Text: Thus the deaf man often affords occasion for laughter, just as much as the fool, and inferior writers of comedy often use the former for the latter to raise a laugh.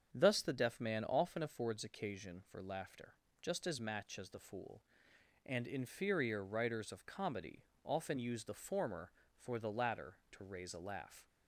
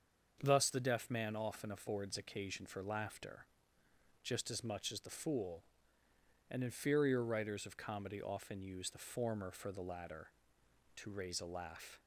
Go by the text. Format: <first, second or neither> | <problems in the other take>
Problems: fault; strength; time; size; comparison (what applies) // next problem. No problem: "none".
second | starts louder than the rest; strong; until 1.1 s; 7 dB; also in the second // says "match" for "much"; at 3.7 s // pauses between "comedy" and "often"; slight; at 7.6 s; 0.20 s long